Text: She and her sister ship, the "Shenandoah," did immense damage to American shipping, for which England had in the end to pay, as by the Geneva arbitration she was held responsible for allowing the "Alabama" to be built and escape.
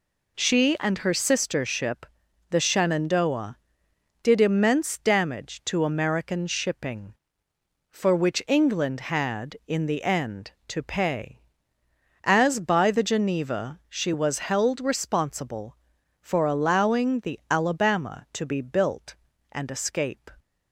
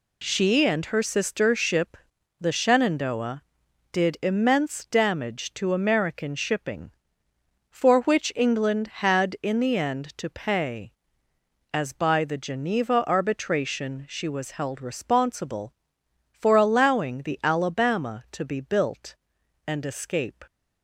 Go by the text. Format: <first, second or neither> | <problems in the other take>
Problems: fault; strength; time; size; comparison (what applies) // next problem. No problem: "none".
second | skips "arbitration"; at 13.8 s